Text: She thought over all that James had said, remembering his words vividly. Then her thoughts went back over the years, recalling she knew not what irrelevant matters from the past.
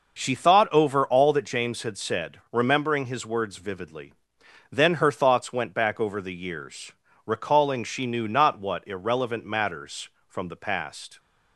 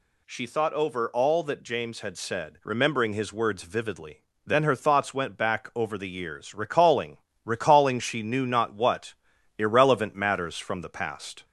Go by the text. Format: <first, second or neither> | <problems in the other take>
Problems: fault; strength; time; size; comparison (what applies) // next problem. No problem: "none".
first | says "recalling" twice; at 7.4 s // pauses between "what" and "irrelevant"; noticeable; at 9.1 s; 0.46 s long